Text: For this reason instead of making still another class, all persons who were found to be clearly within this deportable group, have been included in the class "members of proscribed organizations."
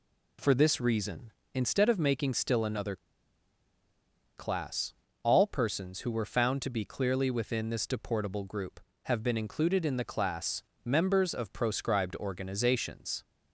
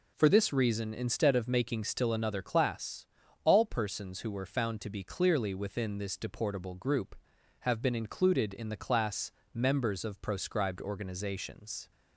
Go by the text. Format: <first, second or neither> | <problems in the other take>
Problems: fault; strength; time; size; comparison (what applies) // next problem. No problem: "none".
second | pauses between "another" and "class"; strong; at 2.9 s; 1.4 s long // pauses between "class" and "members"; slight; at 10.6 s; 0.20 s long; slight in the second